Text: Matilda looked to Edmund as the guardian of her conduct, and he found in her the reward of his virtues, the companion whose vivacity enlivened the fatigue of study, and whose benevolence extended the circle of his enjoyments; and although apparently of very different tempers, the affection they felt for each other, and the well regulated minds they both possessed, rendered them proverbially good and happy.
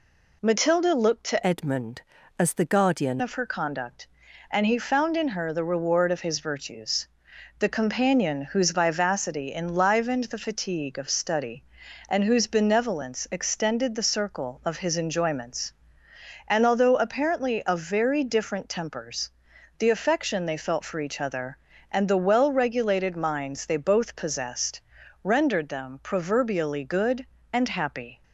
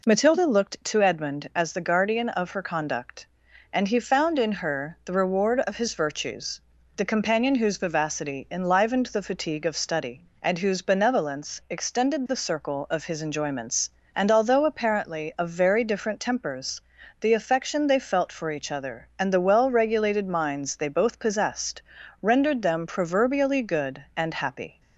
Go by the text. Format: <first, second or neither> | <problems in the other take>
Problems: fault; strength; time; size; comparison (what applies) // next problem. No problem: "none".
second | changes voice from "Edmund" to "guardian"; from 1.4 to 3.2 s; 1.8 s long